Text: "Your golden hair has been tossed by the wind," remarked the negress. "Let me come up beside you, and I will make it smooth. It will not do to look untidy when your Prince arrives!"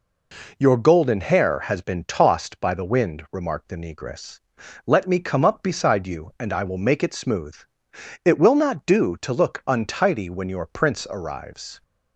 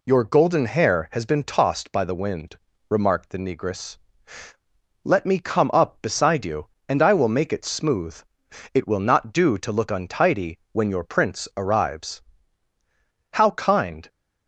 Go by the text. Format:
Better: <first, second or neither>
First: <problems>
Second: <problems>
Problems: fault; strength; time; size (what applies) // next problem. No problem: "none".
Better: first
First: none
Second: pauses between "untidy" and "when"; slight; at 10.5 s; 0.16 s long // goes on to say "How kind"; noticeable; from 13.3 s on; 0.76 s long